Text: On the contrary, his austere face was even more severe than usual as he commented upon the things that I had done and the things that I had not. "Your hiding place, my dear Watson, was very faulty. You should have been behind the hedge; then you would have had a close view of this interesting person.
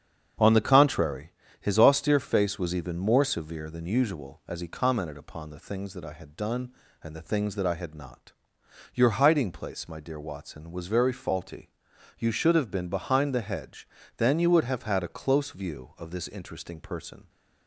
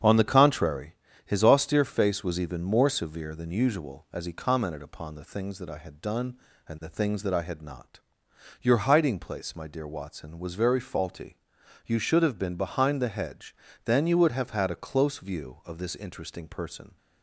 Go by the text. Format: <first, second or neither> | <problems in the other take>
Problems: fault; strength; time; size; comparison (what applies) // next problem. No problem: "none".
neither | starts louder than the rest; strong; the same in both